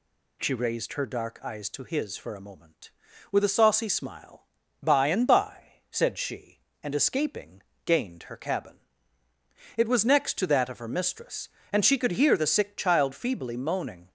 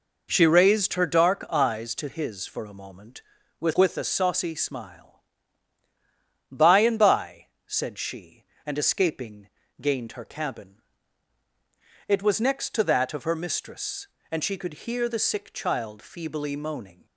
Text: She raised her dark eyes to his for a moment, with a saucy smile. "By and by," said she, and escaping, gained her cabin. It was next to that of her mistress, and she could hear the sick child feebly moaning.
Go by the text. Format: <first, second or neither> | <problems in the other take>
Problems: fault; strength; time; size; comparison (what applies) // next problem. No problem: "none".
first | says "with" twice; at 3.7 s